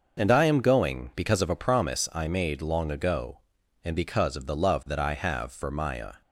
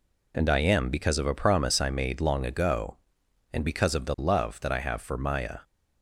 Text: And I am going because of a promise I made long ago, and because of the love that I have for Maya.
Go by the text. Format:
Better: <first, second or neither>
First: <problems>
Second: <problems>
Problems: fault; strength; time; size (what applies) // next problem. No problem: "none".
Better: first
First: none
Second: skips "going"; at 0.8 s